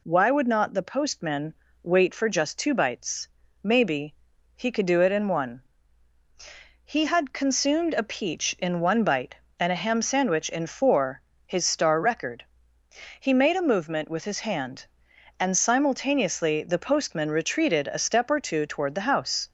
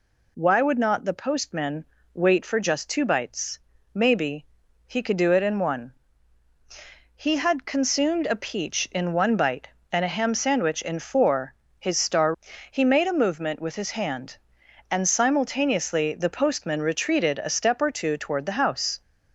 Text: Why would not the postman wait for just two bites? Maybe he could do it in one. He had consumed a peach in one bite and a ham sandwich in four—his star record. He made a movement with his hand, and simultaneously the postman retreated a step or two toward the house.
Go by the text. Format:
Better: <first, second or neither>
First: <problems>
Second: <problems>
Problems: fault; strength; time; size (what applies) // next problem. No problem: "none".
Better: first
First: pauses between "postman" and "wait"; slight; at 1.5 s; 0.28 s long // pauses between "Maybe" and "he"; at 4.1 s; 0.38 s long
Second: pauses between "postman" and "wait"; slight; at 1.8 s; 0.28 s long // pauses between "Maybe" and "he"; at 4.4 s; 0.38 s long // skips "record"; at 12.5 s